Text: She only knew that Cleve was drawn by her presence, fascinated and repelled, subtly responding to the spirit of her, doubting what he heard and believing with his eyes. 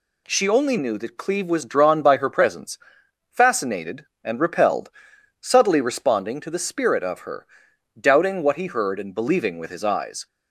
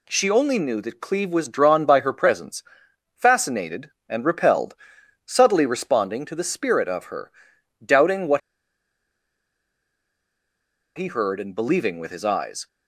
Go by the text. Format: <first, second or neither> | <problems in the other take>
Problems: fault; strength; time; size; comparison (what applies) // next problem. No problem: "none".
first | pauses between "what" and "he"; strong; at 8.4 s; 2.5 s long